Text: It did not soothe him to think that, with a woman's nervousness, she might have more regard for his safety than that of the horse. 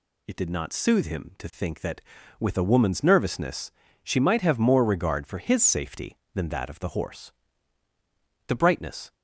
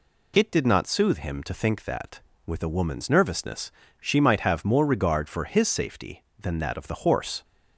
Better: second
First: goes on to say "The brightness"; noticeable; from 8.4 s on; 0.66 s long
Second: none

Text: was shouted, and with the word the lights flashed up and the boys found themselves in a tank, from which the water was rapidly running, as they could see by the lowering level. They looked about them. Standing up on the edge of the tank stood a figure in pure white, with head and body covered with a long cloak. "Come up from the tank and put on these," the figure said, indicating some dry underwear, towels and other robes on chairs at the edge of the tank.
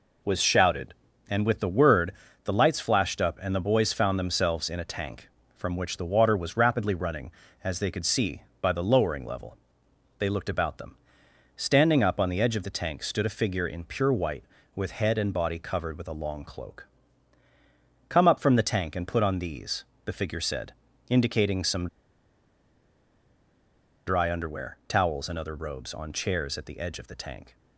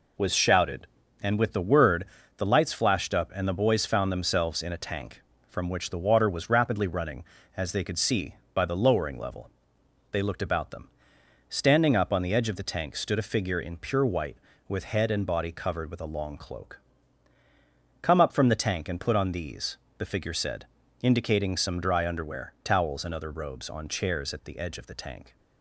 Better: second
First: pauses between "word" and "the"; slight; at 2.1 s; 0.32 s long // pauses between "some" and "dry"; strong; at 21.8 s; 2.1 s long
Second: pauses between "word" and "the"; slight; at 2.0 s; 0.32 s long

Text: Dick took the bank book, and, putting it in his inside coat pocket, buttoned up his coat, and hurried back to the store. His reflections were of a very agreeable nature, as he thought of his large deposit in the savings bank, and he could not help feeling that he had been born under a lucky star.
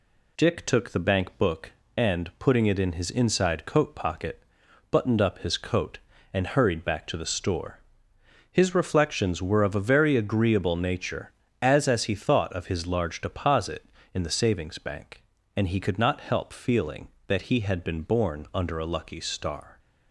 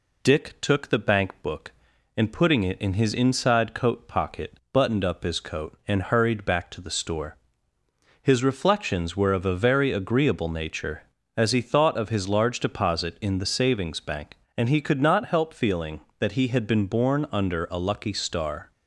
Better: second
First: says "as" twice; at 11.8 s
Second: none

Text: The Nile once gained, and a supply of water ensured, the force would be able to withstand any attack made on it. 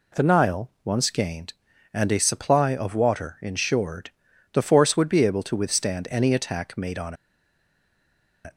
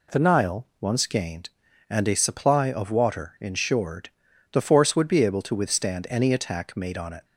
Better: second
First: pauses between "on" and "it"; strong; at 7.1 s; 1.2 s long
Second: none

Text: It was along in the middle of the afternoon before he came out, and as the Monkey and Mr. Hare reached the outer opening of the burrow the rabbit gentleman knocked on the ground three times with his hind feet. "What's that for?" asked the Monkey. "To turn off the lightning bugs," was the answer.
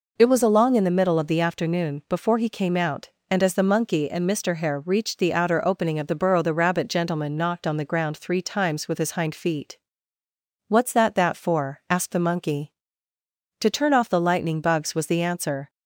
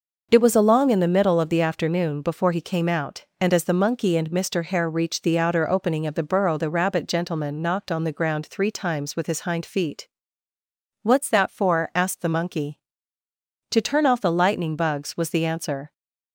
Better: second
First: says "that" twice; at 11.1 s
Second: none

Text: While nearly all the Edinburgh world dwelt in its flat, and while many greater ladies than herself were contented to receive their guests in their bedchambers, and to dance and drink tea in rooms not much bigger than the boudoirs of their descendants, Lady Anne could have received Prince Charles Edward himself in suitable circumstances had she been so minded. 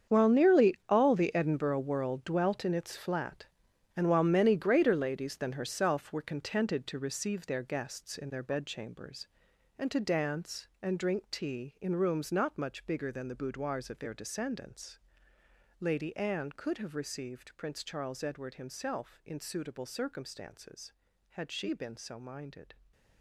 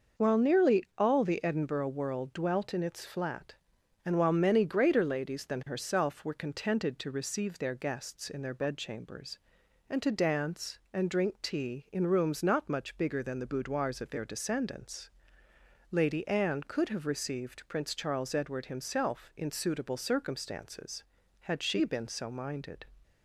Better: second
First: gets quieter; strong; throughout; 14 dB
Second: none

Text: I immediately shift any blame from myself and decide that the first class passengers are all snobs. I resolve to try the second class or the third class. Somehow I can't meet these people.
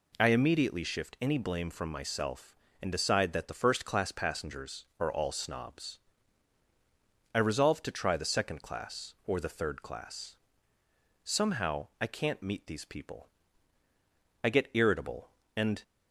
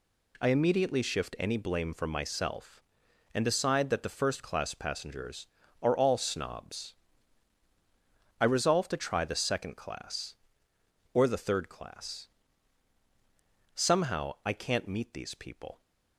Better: second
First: goes on to say "I get irritable and"; from 14.4 s on; 1.4 s long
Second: none

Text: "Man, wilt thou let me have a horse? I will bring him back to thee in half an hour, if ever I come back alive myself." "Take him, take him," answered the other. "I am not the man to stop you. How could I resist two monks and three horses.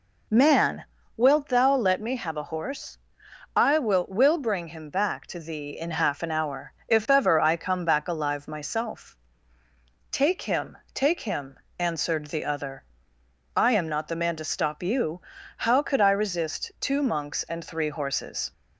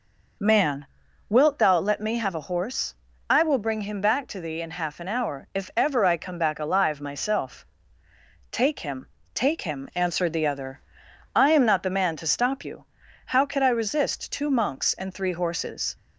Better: second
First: says "will" twice; at 4.0 s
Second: none

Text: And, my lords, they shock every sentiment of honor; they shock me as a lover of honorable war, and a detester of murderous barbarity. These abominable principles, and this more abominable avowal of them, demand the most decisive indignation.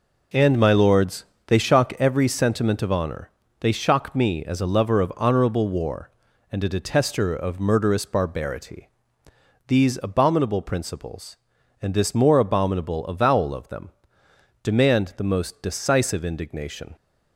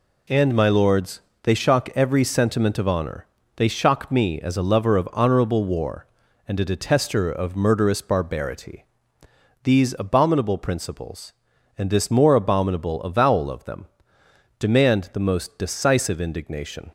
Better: second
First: starts louder than the rest; noticeable; until 2.2 s; 5 dB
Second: none

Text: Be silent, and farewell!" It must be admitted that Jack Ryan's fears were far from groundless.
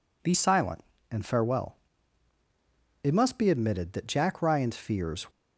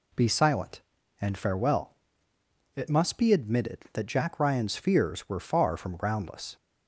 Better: second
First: stops before "were far from groundless"; at 5.3 s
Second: none

